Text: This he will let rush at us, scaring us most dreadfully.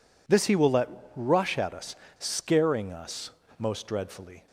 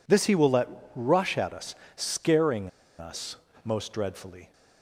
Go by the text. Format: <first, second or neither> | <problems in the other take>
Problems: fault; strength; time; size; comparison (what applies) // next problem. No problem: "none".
first | pauses between "let" and "rush"; slight; at 0.6 s; 0.28 s long; slight in the first // pauses between "scaring" and "us"; slight; at 2.6 s; 0.29 s long // pauses between "us" and "most"; slight; at 3.3 s; 0.28 s long; slight in the first